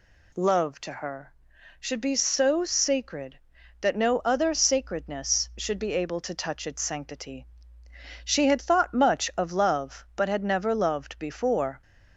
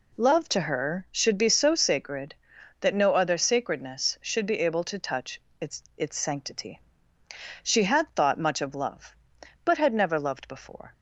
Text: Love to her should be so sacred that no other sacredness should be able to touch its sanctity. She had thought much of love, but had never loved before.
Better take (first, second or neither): first